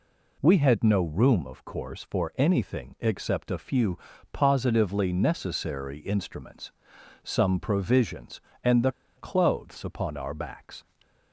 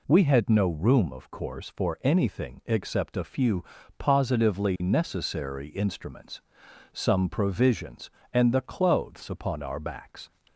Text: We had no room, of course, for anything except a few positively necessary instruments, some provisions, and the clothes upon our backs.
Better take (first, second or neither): second